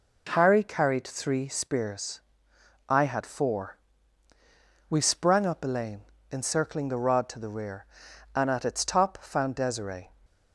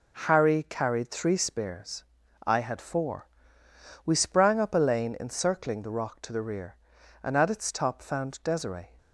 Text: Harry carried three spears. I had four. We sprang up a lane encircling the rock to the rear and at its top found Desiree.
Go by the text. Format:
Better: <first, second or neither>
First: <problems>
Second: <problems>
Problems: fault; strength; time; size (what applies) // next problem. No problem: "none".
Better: second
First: pauses between "lane" and "encircling"; slight; at 6.0 s; 0.30 s long // says "rod" for "rock"; at 6.9 s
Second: none